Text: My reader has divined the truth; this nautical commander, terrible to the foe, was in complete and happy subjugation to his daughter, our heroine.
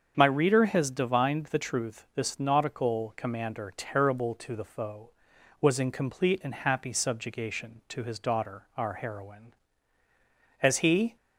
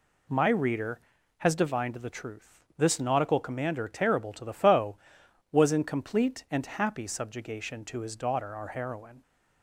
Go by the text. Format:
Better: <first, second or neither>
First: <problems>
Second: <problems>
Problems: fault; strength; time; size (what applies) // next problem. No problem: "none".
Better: second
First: starts louder than the rest; strong; until 1.1 s; 7 dB // goes on to say "As he"; from 10.6 s on; 0.54 s long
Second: none